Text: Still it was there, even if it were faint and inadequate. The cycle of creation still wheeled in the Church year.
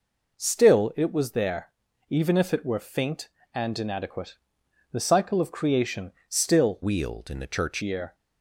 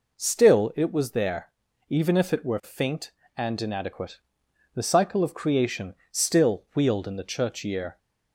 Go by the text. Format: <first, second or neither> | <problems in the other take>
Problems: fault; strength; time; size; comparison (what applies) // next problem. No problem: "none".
second | pauses between "creation" and "still"; slight; at 6.1 s; 0.16 s long; slight in the second // changes voice from "wheeled" to "Church"; from 6.8 to 7.8 s; 1.0 s long